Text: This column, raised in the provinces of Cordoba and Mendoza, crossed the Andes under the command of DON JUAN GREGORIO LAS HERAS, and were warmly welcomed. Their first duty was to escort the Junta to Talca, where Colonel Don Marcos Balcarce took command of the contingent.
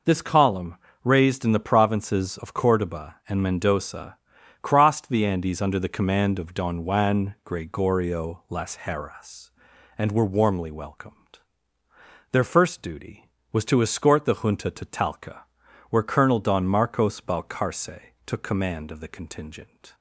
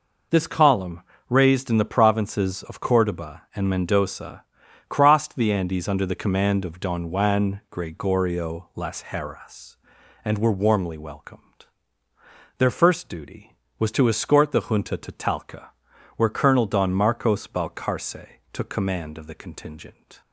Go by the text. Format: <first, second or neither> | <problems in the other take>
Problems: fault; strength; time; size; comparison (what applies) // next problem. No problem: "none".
neither | pauses between "Balcarce" and "took"; slight; the same in both